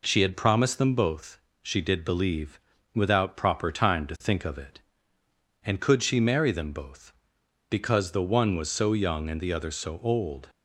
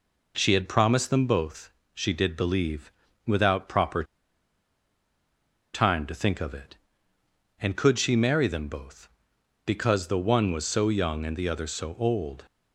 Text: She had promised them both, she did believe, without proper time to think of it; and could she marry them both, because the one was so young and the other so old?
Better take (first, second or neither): first